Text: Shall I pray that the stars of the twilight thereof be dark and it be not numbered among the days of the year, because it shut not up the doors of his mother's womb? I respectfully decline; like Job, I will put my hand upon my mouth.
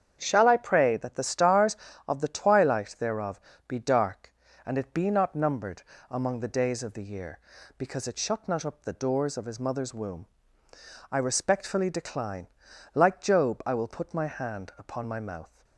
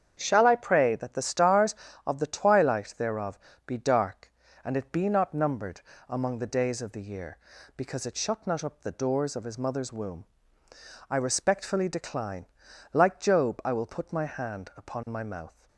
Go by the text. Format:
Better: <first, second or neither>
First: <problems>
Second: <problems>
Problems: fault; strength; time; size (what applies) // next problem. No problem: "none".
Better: neither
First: starts louder than the rest; strong; until 1.2 s; 8 dB // pauses between "thereof" and "be"; slight; at 3.3 s; 0.30 s long // pauses between "numbered" and "among"; slight; at 5.8 s; 0.28 s long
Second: starts louder than the rest; strong; until 1.2 s; 8 dB // pauses between "thereof" and "be"; slight; at 3.3 s; 0.30 s long // pauses between "numbered" and "among"; slight; at 5.8 s; 0.28 s long